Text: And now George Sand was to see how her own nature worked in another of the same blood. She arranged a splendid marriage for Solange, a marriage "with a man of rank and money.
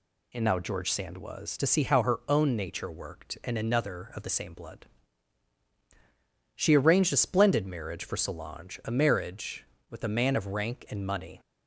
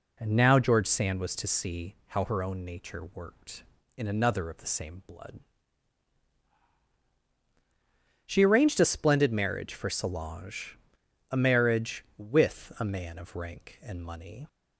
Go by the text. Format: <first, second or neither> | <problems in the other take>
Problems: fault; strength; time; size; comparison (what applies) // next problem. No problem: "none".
neither | none